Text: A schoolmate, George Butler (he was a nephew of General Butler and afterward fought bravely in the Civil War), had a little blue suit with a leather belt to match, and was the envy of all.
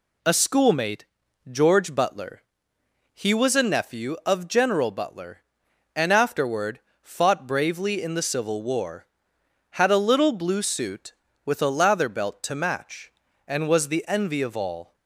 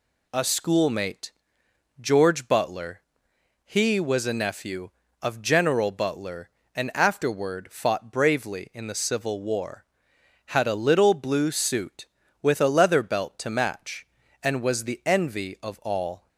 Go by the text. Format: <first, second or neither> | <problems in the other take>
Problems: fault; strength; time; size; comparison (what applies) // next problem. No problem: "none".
second | pauses between "afterward" and "fought"; slight; at 6.7 s; 0.22 s long // says "lather" for "leather"; at 11.7 s